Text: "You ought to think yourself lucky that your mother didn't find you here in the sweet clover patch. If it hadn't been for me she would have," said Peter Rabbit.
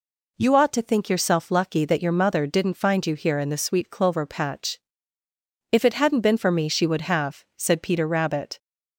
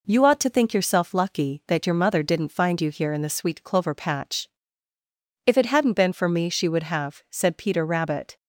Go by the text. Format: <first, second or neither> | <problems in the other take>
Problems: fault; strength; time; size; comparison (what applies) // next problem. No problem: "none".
neither | none